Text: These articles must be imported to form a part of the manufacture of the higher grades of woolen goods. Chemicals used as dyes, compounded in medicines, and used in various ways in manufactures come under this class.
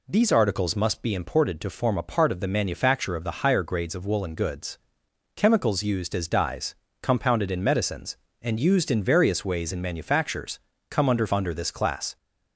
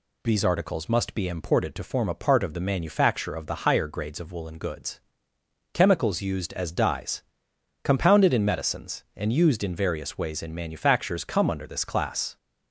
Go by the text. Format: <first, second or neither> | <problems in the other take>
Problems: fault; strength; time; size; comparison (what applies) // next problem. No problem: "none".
second | pauses between "manufactures" and "come"; slight; at 10.6 s; 0.28 s long // says "under" twice; at 11.3 s